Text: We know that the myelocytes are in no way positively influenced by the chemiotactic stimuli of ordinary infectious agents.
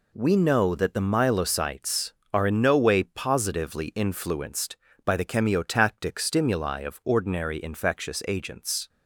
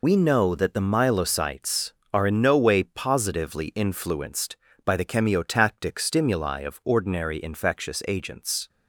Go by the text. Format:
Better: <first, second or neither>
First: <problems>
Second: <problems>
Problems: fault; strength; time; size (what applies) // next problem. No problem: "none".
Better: first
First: none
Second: loses the start of "We"; at 0.0 s; 90 ms